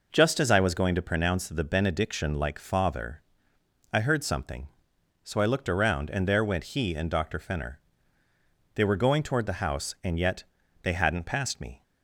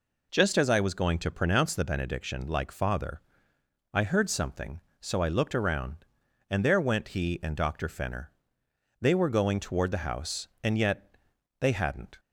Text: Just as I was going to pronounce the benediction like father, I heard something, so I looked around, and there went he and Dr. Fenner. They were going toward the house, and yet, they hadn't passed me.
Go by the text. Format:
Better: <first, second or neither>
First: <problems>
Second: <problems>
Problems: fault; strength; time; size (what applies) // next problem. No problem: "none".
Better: first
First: none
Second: stops before "passed me"; at 12.1 s